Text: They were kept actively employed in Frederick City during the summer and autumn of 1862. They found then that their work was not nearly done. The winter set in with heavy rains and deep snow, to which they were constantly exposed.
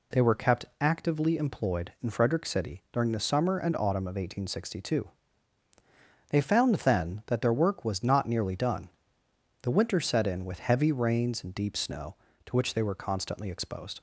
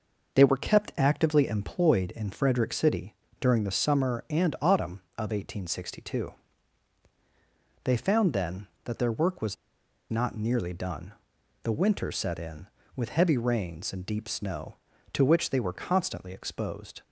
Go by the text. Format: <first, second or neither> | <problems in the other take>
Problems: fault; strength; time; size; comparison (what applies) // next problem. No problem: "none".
first | pauses between "City" and "during"; slight; at 3.1 s; 0.24 s long // pauses between "was" and "not"; noticeable; at 9.5 s; 0.54 s long